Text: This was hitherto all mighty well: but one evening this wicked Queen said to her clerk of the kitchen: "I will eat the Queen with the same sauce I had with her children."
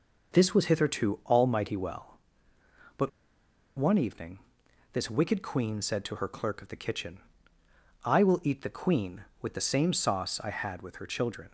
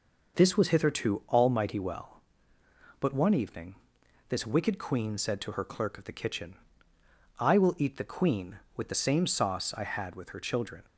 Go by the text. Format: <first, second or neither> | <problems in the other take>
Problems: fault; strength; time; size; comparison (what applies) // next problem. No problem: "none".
second | pauses between "but" and "one"; noticeable; at 3.0 s; 0.67 s long // pauses between "evening" and "this"; noticeable; at 4.3 s; 0.52 s long; noticeable in the second